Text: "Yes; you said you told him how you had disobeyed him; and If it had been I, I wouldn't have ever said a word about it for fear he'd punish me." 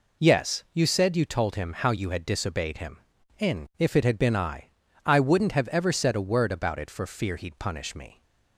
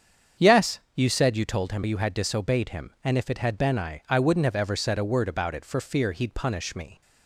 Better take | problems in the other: first | starts louder than the rest; strong; until 1.5 s; 7.5 dB // skips "how"; at 1.8 s

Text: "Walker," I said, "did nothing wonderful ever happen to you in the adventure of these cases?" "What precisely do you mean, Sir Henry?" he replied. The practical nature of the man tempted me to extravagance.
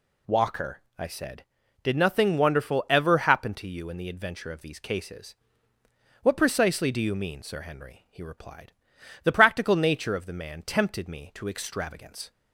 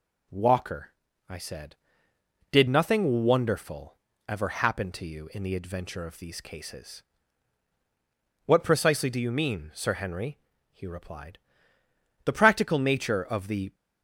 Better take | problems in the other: first | pauses between "wonderful" and "ever"; slight; at 3.9 s; 0.30 s long // stops before "man tempted me to extravagance"; at 13.7 s

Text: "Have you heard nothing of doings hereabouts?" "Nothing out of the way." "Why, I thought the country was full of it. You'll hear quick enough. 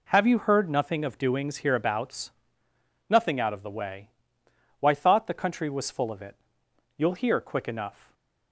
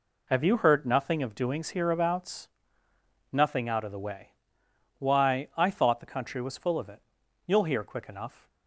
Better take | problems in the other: second | skips "I"; at 4.9 s // stays silent after the last word; slight; from 7.9 s on; 0.6 s long

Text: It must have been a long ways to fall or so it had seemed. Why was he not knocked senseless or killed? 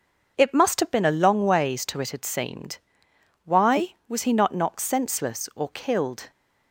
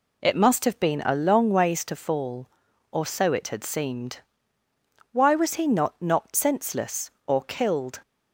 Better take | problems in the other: second | starts louder than the rest; until 1.3 s; 6 dB // skips "fall or so"; at 2.0 s

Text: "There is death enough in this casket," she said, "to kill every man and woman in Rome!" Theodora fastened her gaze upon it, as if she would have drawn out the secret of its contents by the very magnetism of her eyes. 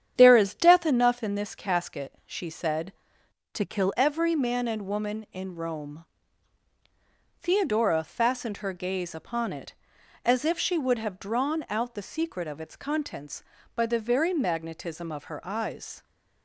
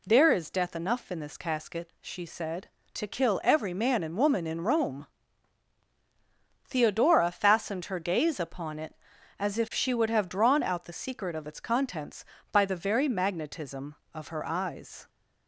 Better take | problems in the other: second | starts louder than the rest; strong; until 1.1 s; 9 dB // changes voice from "to" to "kill"; from 3.5 to 3.9 s; 0.4 s long

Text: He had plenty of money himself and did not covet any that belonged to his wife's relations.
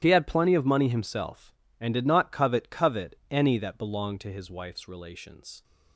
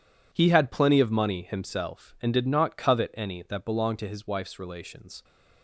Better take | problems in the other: second | starts louder than the rest; strong; until 1.0 s; 11 dB // says "covet" twice; at 2.6 s

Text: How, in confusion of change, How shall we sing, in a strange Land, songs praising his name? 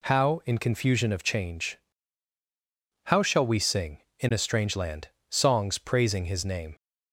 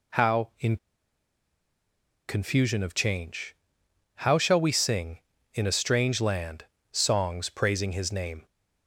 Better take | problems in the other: first | pauses between "in" and "confusion"; strong; at 0.7 s; 1.5 s long

